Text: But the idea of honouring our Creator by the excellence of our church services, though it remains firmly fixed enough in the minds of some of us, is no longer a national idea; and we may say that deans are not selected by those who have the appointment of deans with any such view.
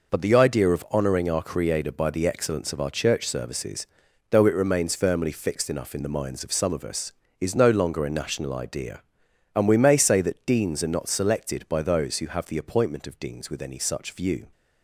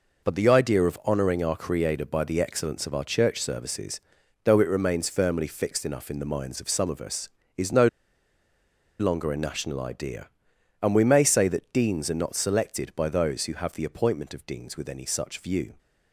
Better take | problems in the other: first | pauses between "no" and "longer"; at 7.8 s; 1.1 s long

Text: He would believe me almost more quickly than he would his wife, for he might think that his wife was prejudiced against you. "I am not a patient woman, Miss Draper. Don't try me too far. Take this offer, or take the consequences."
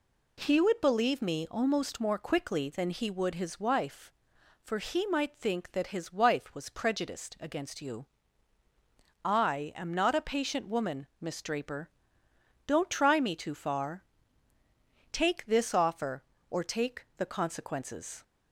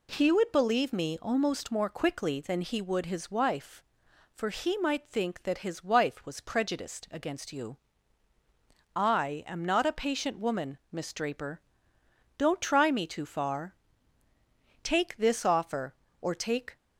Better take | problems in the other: first | stops before "the consequences"; at 16.7 s

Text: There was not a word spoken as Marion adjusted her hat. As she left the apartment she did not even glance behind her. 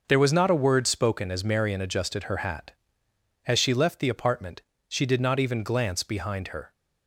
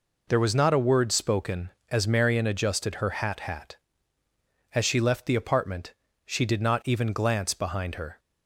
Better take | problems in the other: first | says "hat" twice; at 3.4 s // pauses between "apartment" and "she"; slight; at 5.9 s; 0.32 s long; slight in the first

